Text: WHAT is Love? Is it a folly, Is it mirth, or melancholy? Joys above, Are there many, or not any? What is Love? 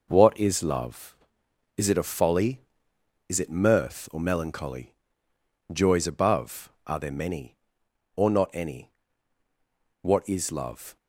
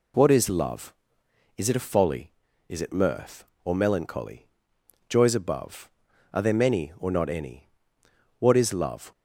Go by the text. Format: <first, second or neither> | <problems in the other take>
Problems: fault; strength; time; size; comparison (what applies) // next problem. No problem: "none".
second | gets quieter; strong; throughout; 7.5 dB